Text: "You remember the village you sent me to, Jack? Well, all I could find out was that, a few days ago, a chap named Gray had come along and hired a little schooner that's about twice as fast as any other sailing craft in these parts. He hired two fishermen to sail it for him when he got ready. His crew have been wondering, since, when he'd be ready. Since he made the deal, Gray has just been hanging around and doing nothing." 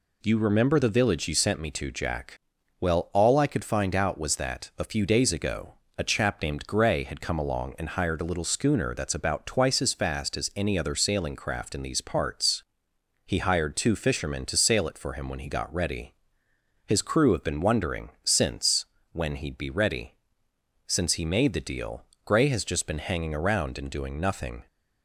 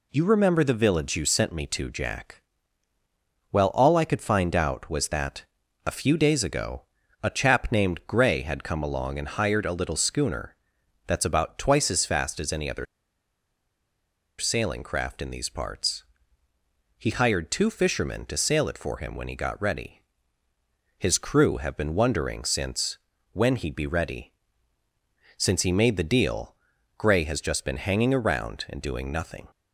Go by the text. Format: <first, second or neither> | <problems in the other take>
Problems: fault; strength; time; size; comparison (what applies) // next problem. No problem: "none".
first | pauses between "schooner" and "that's"; noticeable; at 10.5 s; 0.50 s long // pauses between "other" and "sailing"; strong; at 12.8 s; 1.5 s long